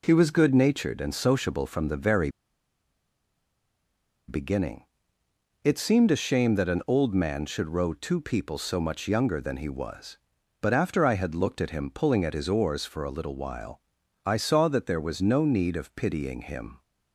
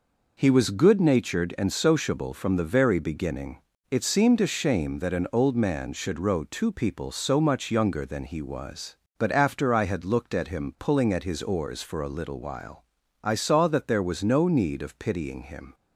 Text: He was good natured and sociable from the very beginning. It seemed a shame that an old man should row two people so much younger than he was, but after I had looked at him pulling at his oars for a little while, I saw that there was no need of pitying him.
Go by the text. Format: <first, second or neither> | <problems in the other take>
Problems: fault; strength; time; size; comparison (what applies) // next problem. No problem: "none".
second | pauses between "very" and "beginning"; strong; at 2.2 s; 1.9 s long